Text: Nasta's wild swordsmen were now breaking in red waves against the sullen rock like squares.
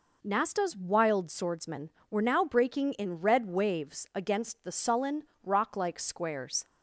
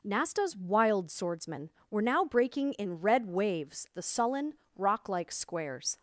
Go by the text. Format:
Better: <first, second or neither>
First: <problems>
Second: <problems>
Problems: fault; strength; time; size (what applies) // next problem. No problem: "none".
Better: first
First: pauses between "sullen" and "rock"; slight; at 5.2 s; 0.22 s long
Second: skips "against"; at 3.9 s // pauses between "sullen" and "rock"; slight; at 4.5 s; 0.24 s long